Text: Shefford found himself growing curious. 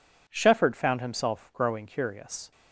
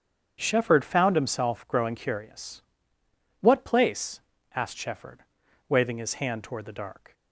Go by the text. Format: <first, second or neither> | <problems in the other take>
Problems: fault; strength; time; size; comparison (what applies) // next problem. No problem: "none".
first | starts louder than the rest; strong; until 1.4 s; 7.5 dB // goes on to say "What place asked Shefford waving his hand toward the dark"; strong; from 3.4 s on; 3.7 s long